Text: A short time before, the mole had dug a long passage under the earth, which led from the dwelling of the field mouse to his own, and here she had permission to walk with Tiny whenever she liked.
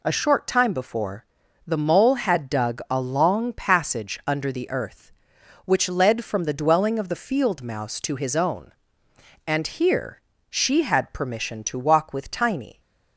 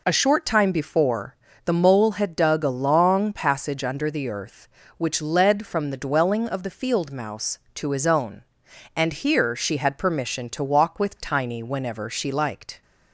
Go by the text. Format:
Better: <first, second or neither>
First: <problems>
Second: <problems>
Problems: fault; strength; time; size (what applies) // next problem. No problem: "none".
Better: second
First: pauses between "here" and "she"; slight; at 10.2 s; 0.28 s long // stops before "whenever she liked"; at 12.7 s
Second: none